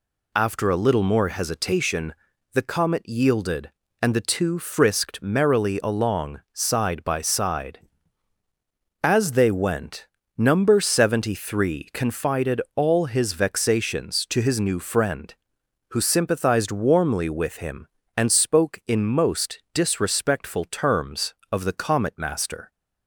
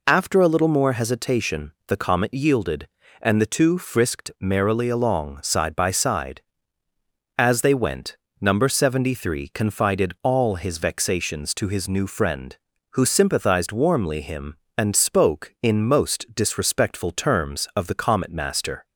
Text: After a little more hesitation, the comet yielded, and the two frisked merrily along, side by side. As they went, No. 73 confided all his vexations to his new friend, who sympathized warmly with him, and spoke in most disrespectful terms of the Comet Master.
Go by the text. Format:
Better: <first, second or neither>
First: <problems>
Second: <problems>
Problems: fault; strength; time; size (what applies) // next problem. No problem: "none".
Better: first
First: none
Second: skips "with"; at 14.2 s